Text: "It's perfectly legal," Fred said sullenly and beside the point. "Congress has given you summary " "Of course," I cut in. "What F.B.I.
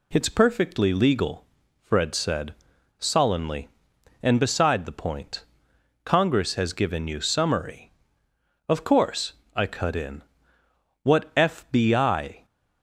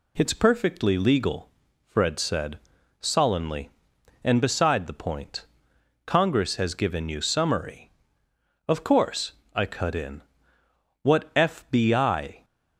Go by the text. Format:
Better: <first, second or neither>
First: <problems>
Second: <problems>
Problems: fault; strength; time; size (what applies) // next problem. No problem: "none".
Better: neither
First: pauses between "said" and "sullenly"; at 2.5 s; 0.45 s long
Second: pauses between "said" and "sullenly"; at 2.5 s; 0.42 s long